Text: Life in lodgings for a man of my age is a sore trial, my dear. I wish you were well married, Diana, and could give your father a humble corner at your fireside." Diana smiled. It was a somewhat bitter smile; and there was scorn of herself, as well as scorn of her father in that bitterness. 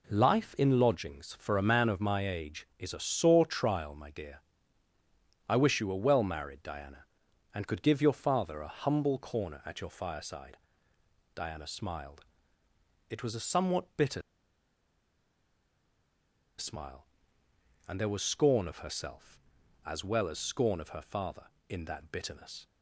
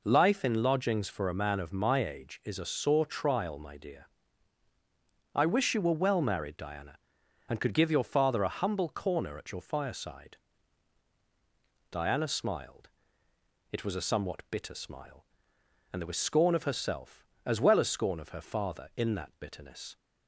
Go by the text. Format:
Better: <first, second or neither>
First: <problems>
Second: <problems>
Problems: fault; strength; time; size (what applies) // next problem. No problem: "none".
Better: second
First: pauses between "bitter" and "smile"; strong; at 14.2 s; 2.3 s long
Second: none